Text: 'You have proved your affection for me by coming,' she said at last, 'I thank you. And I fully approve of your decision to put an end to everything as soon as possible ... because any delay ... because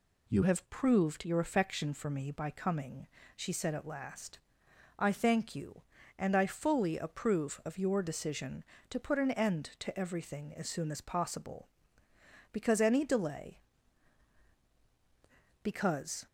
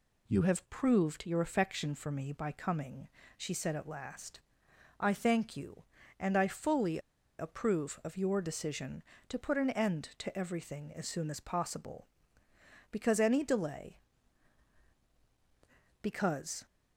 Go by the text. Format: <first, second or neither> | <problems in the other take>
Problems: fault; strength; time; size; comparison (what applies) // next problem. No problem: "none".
first | pauses between "fully" and "approve"; at 6.9 s; 0.40 s long